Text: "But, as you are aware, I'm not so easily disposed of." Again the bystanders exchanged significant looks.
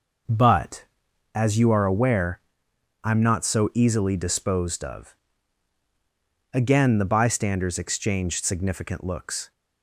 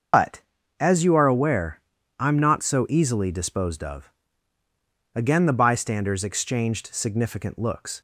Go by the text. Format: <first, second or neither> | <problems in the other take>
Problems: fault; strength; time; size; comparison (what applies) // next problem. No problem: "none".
first | loses the start of "But"; at 0.1 s; 110 ms // starts louder than the rest; until 1.5 s; 6.5 dB